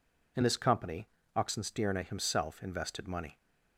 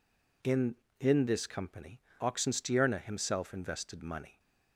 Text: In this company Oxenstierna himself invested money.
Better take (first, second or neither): first